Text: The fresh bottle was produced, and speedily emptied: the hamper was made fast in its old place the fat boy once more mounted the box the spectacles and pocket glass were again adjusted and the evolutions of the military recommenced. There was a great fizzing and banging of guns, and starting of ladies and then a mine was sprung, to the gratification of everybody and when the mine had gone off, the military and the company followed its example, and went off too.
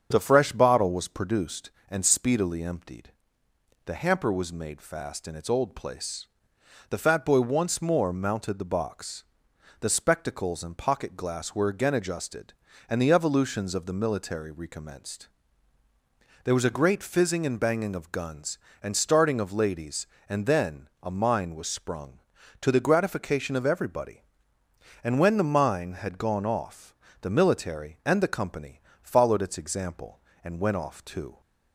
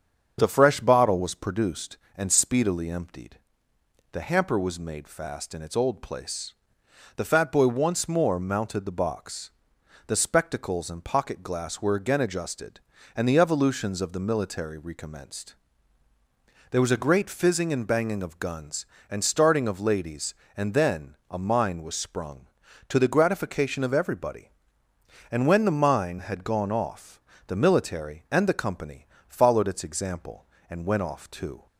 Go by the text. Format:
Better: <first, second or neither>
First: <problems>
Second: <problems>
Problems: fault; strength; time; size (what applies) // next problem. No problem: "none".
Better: neither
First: starts louder than the rest; until 1.1 s; 7 dB // pauses between "place" and "the"; noticeable; at 6.2 s; 0.62 s long // pauses between "box" and "the"; noticeable; at 9.2 s; 0.56 s long // pauses between "then" and "a"; slight; at 20.8 s; 0.16 s long // pauses between "company" and "followed"; slight; at 28.8 s; 0.22 s long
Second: starts louder than the rest; until 1.4 s; 7 dB // pauses between "place" and "the"; noticeable; at 6.5 s; 0.62 s long // pauses between "box" and "the"; noticeable; at 9.4 s; 0.56 s long // pauses between "then" and "a"; slight; at 21.1 s; 0.16 s long // pauses between "company" and "followed"; slight; at 29.0 s; 0.22 s long